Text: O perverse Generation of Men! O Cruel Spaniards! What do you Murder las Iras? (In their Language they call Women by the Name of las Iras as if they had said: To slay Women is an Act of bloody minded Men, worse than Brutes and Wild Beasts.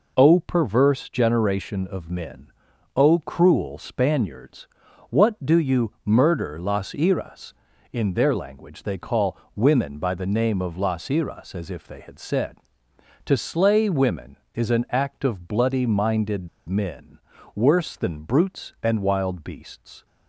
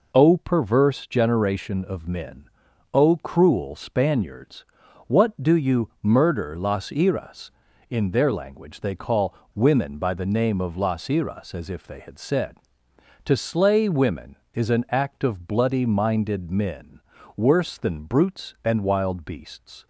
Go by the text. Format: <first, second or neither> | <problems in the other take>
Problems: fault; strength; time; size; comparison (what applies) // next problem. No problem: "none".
second | pauses between "call" and "Women"; slight; at 9.3 s; 0.18 s long; slight in the second // pauses between "minded" and "Men"; slight; at 16.4 s; 0.20 s long